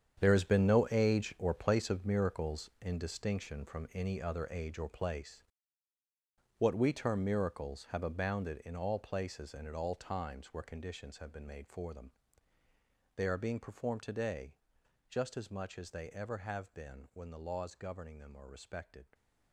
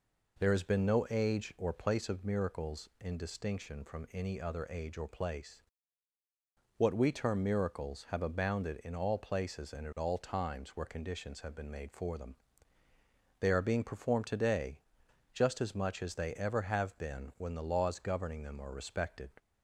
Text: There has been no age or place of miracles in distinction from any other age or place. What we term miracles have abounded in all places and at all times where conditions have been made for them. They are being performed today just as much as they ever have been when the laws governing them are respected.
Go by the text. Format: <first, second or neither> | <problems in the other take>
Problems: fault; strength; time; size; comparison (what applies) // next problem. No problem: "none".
second | gets quieter; strong; throughout; 13 dB // pauses between "today" and "just"; noticeable; at 14.5 s; 0.54 s long; noticeable in the second